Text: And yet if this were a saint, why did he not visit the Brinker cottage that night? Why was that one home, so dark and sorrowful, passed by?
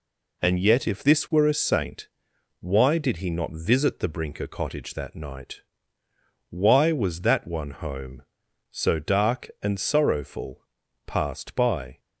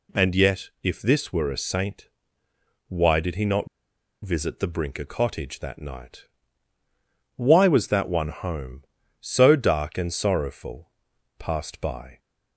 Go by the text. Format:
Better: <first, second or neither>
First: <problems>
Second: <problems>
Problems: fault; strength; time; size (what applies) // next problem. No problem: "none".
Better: first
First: none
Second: pauses between "not" and "visit"; noticeable; at 3.6 s; 0.57 s long